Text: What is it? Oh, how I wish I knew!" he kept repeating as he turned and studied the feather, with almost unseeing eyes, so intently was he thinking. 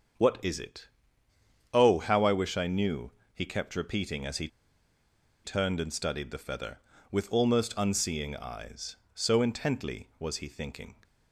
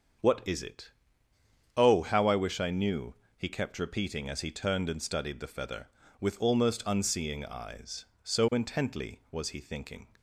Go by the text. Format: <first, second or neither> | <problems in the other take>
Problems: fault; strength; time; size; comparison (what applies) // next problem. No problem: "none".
second | starts louder than the rest; until 2.0 s; 6.5 dB; also in the second // pauses between "he" and "turned"; noticeable; at 4.4 s; 0.96 s long